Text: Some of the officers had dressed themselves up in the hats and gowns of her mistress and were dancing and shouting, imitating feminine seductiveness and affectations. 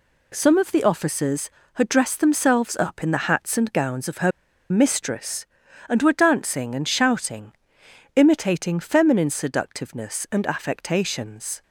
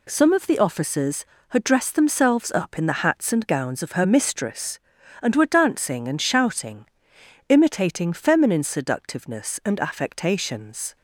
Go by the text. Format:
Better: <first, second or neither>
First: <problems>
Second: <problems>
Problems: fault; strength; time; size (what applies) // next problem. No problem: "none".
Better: second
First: pauses between "her" and "mistress"; at 4.3 s; 0.41 s long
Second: none